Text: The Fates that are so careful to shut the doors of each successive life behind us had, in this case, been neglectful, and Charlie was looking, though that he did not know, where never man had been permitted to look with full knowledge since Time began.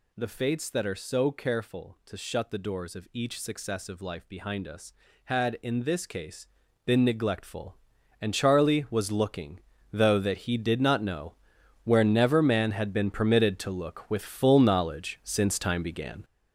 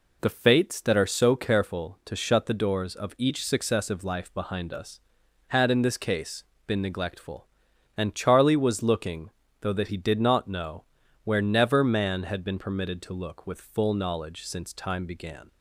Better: second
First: gets louder; strong; throughout; 8 dB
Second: none

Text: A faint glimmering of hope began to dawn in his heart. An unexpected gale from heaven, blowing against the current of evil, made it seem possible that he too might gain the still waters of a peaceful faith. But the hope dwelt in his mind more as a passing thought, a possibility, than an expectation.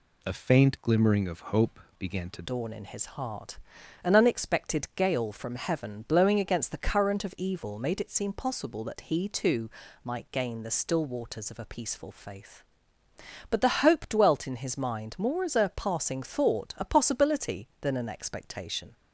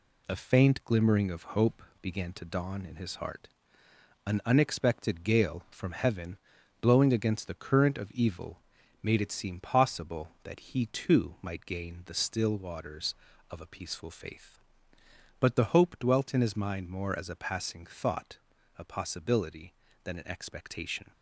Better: second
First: pauses between "hope" and "began"; slight; at 1.7 s; 0.18 s long // changes voice at "dawn"; from 2.4 s on; 16.5 s long // pauses between "too" and "might"; slight; at 9.6 s; 0.34 s long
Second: pauses between "hope" and "began"; slight; at 1.8 s; 0.18 s long

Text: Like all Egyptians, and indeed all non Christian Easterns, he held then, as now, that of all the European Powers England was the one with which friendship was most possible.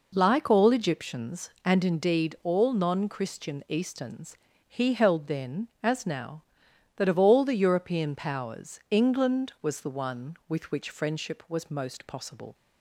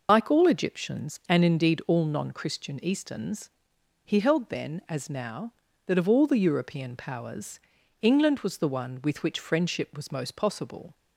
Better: first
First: none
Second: loses the start of "Like"; at 0.0 s; 55 ms // pauses between "Powers" and "England"; at 7.5 s; 0.42 s long

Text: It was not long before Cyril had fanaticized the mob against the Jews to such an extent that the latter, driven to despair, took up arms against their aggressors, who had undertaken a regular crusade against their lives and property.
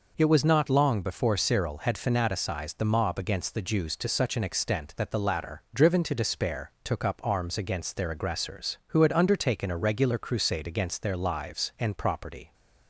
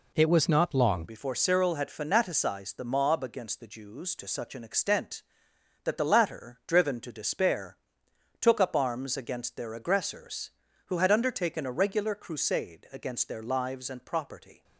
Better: first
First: none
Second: changes voice at "before"; from 1.0 s on; 13.6 s long

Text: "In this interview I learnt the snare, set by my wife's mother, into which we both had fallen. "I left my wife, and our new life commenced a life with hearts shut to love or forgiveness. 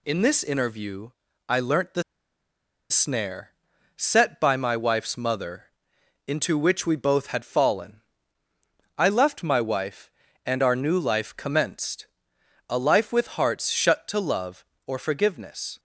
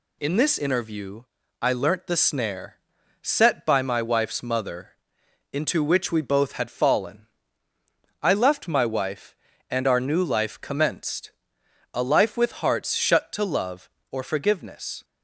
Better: second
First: pauses between "interview" and "I"; slight; at 1.1 s; 0.36 s long // pauses between "the" and "snare"; noticeable; at 2.0 s; 0.88 s long // pauses between "commenced" and "a"; noticeable; at 12.0 s; 0.62 s long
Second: pauses between "interview" and "I"; slight; at 1.2 s; 0.36 s long // pauses between "commenced" and "a"; noticeable; at 11.3 s; 0.62 s long

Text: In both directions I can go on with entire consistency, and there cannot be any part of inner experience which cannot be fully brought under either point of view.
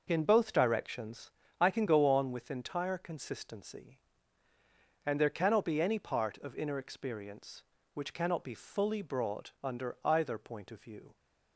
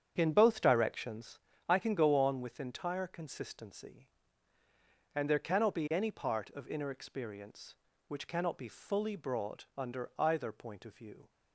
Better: first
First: pauses between "directions" and "I"; slight; at 1.3 s; 0.30 s long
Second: starts louder than the rest; strong; until 1.3 s; 8.5 dB // pauses between "directions" and "I"; slight; at 1.3 s; 0.30 s long

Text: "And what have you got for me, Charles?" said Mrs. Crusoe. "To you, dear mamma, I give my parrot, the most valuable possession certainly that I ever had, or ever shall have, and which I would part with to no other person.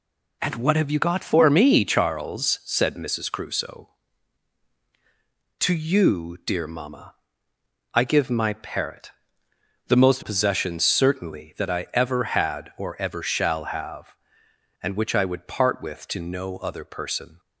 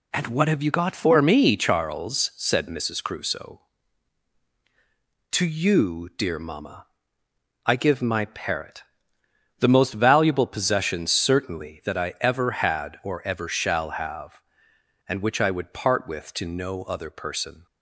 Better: second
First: skips "valuable"; at 10.2 s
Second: none

